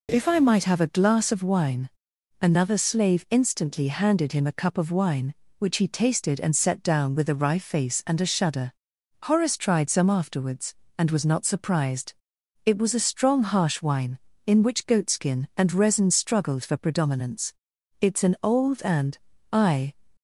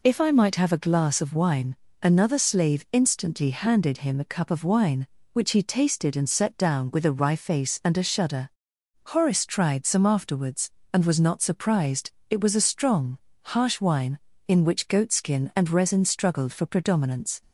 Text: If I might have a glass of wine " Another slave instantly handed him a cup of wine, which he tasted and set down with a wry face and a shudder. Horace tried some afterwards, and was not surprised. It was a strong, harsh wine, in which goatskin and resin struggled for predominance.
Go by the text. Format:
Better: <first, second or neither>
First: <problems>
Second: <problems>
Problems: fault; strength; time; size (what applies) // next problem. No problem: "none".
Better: second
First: goes on to say "It's an old and I"; strong; from 18.0 s on; 1.9 s long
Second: none